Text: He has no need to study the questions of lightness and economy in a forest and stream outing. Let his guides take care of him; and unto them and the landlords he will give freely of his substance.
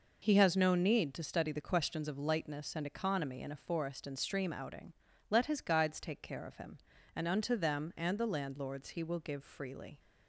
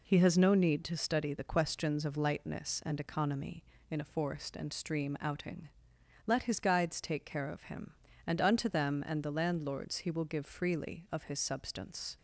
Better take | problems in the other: second | stops before "of his substance"; at 9.9 s

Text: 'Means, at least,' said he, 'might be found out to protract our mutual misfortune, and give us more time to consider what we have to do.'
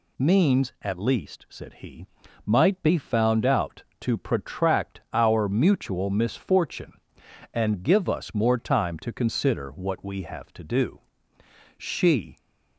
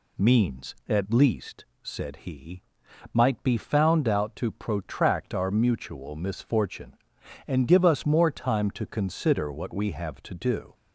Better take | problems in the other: second | goes on to say "She"; from 11.7 s on; 0.60 s long

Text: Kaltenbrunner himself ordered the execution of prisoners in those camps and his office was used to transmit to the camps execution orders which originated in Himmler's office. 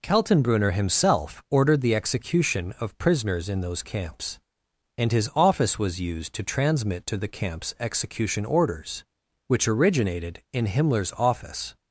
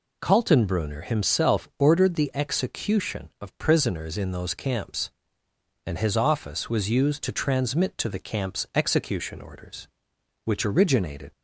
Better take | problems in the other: first | stops before "in Himmler's office"; at 11.3 s

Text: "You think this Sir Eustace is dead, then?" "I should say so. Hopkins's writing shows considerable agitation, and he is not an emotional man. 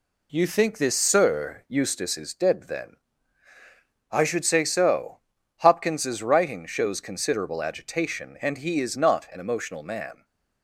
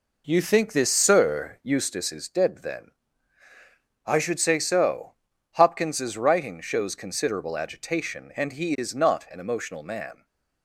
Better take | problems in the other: first | starts louder than the rest; noticeable; until 1.9 s; 4.5 dB // stays silent after the last word; slight; from 10.1 s on; 0.5 s long; slight in the first

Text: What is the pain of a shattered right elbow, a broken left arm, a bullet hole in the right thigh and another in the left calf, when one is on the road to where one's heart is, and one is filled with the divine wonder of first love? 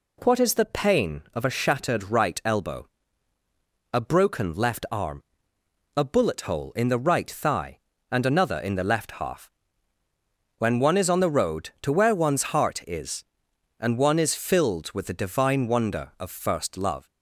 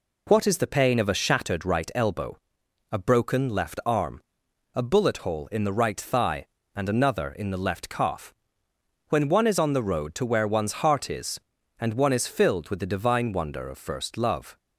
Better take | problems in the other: second | says "half" for "calf"; at 9.1 s

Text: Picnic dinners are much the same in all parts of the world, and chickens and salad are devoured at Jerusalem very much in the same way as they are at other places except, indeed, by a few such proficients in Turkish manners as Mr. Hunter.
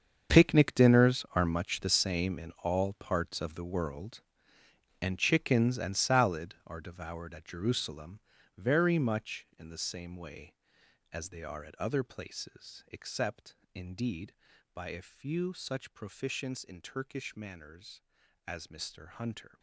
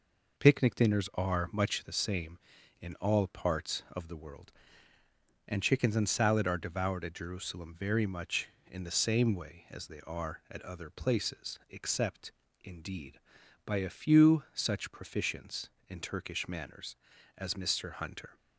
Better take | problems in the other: second | gets quieter; strong; throughout; 14.5 dB // pauses between "Jerusalem" and "very"; slight; at 8.2 s; 0.36 s long

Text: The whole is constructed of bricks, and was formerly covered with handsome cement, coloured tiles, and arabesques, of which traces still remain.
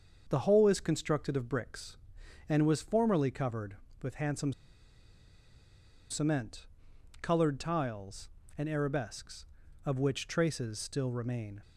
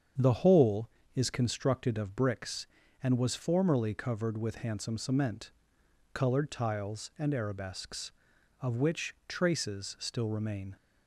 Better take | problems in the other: second | starts louder than the rest; until 1.2 s; 6.5 dB; strong in the second // pauses between "handsome" and "cement"; strong; at 4.5 s; 1.5 s long

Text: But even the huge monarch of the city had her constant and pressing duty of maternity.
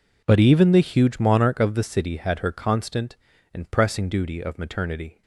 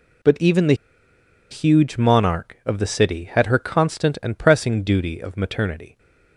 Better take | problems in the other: first | pauses between "the" and "huge"; noticeable; at 0.7 s; 0.77 s long

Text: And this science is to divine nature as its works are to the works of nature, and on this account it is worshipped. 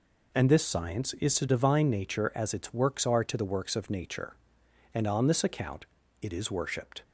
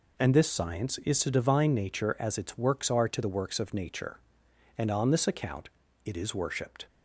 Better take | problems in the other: neither | pauses between "account" and "it"; slight; the same in both

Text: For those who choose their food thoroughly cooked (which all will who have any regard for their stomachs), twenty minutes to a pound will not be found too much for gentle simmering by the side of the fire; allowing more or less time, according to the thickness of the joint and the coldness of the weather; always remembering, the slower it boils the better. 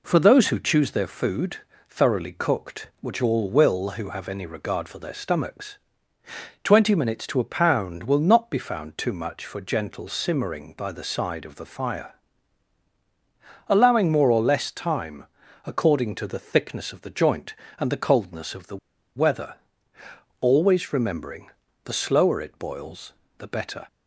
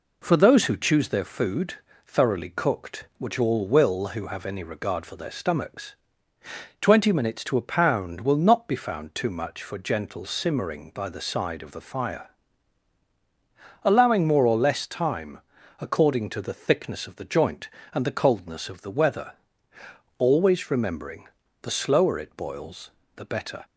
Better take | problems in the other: second | pauses between "food" and "thoroughly"; slight; at 1.5 s; 0.32 s long; slight in the second // pauses between "the" and "weather"; at 18.7 s; 0.36 s long // pauses between "boils" and "the"; slight; at 23.1 s; 0.26 s long; slight in the second

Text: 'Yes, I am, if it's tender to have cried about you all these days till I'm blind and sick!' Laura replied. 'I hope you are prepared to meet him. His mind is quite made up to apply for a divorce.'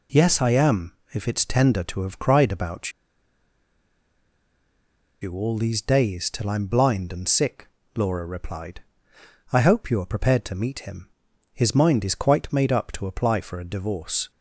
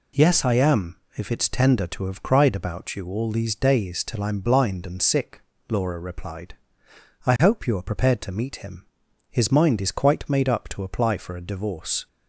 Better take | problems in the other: second | pauses between "about" and "you"; strong; at 2.9 s; 2.3 s long

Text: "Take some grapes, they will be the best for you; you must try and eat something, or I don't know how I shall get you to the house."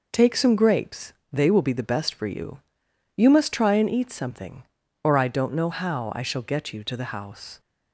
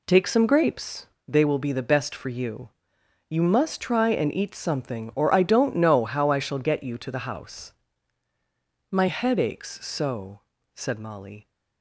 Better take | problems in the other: first | goes on to say "My head aches so said Molly"; strong; from 8.9 s on; 2.5 s long

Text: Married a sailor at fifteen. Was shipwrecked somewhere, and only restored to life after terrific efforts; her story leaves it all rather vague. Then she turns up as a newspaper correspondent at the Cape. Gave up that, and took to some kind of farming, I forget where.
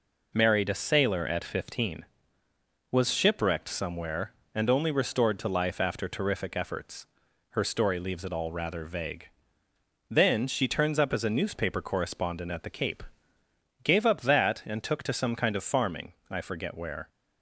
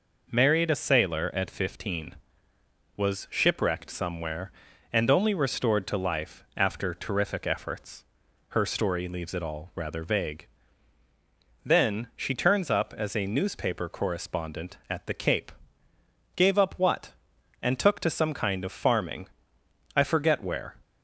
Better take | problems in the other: first | says "what" for "that"; at 16.7 s

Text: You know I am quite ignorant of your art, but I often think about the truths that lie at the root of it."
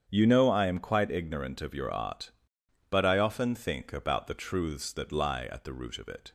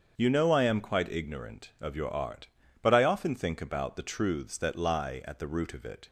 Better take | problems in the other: neither | starts louder than the rest; the same in both

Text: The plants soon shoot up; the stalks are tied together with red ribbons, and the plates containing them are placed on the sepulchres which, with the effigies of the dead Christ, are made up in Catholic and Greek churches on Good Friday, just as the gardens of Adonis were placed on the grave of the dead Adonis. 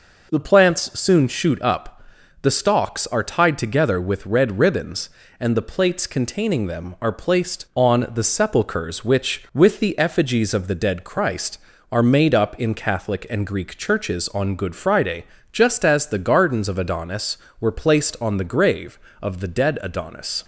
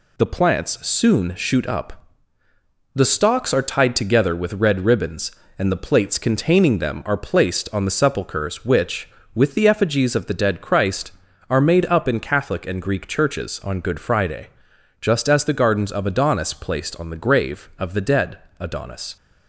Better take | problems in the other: first | skips "were"; at 16.5 s // pauses between "dead" and "Adonis"; slight; at 18.3 s; 0.22 s long

